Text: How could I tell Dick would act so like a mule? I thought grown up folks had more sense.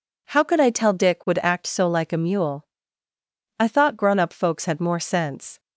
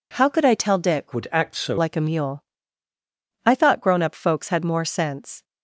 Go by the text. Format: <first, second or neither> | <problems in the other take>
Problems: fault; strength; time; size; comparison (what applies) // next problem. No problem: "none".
first | changes voice from "would" to "so"; from 1.1 to 1.7 s; 0.6 s long